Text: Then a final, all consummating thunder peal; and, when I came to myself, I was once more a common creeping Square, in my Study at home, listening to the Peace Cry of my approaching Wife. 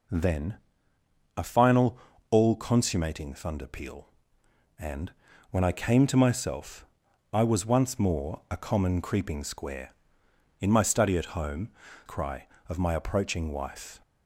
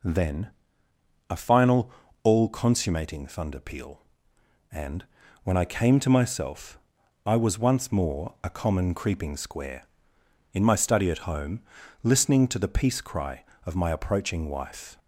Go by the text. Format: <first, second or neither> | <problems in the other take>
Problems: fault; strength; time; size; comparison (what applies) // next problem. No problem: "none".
second | pauses between "Then" and "a"; noticeable; at 0.5 s; 0.80 s long; noticeable in the second // skips "listening to the Peace"; at 11.8 s